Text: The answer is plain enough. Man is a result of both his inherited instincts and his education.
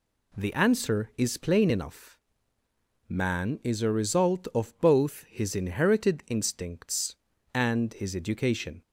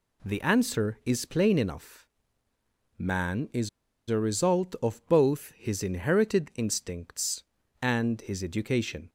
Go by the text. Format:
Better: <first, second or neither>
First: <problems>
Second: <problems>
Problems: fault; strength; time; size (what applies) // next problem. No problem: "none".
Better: first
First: none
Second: pauses between "is" and "a"; at 3.6 s; 0.39 s long